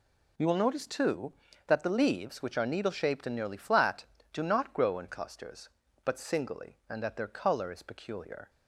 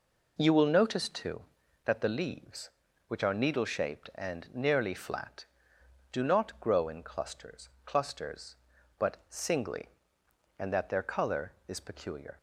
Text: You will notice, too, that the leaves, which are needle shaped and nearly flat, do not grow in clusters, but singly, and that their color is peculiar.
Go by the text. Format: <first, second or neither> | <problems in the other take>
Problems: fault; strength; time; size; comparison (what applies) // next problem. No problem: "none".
first | says "clusters" twice; at 7.8 s